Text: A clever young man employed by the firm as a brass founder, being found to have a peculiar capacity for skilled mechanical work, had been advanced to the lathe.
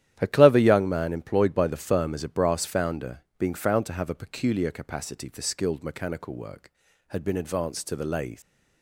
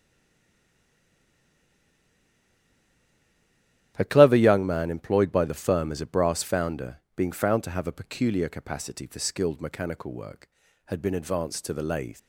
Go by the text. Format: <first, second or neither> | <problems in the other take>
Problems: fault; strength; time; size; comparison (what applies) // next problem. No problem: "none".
first | stays silent before the first word; strong; until 3.9 s; 3.9 s long // starts louder than the rest; strong; until 4.9 s; 11.5 dB; strong in the first